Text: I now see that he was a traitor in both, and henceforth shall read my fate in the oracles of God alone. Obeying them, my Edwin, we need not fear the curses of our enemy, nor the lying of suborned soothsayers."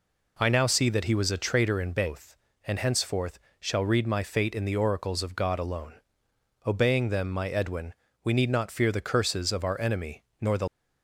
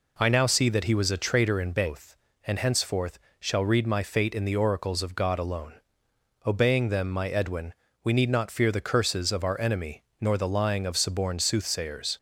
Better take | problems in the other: second | pauses between "henceforth" and "shall"; slight; at 3.3 s; 0.20 s long; slight in the second // stops before "lying of suborned soothsayers"; at 10.6 s

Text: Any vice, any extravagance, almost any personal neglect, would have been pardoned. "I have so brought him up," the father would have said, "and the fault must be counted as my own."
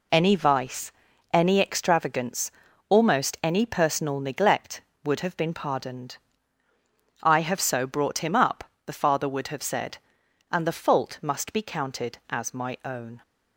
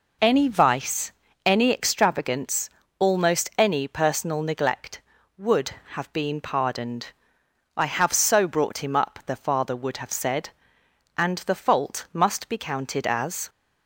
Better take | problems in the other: first | stops before "my own"; at 13.4 s

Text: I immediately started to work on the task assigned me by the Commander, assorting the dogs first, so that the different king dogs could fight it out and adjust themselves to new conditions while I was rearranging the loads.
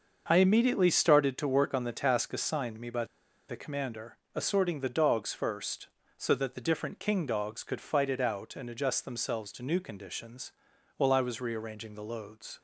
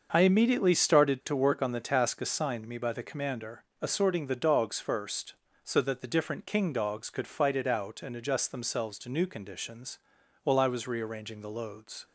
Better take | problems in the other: second | starts louder than the rest; until 1.2 s; 6.5 dB; also in the second // pauses between "by" and "the"; at 3.0 s; 0.43 s long // pauses between "conditions" and "while"; noticeable; at 10.5 s; 0.46 s long; noticeable in the second

